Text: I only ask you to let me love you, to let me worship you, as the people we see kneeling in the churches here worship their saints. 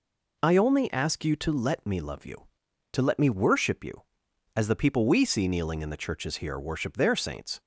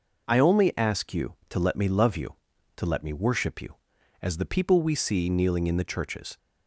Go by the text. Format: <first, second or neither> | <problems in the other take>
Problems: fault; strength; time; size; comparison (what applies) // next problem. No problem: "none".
first | stops before "here worship their saints"; at 6.3 s